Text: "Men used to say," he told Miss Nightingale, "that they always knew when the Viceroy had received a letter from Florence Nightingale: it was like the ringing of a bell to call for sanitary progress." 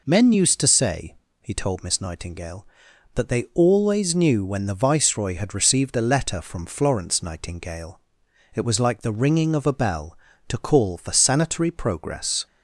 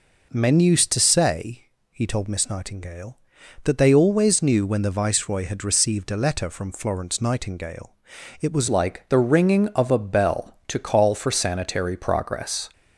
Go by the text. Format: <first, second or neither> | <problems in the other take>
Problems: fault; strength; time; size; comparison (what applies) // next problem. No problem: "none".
first | changes voice at "like"; from 8.6 s on; 4.0 s long